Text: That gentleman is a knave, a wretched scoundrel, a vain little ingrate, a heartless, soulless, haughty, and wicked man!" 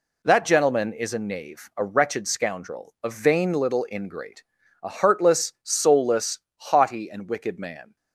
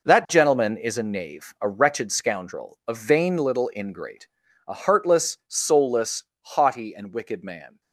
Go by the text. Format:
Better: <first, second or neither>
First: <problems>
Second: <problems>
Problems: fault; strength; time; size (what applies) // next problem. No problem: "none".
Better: first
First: none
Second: gets quieter; strong; throughout; 10.5 dB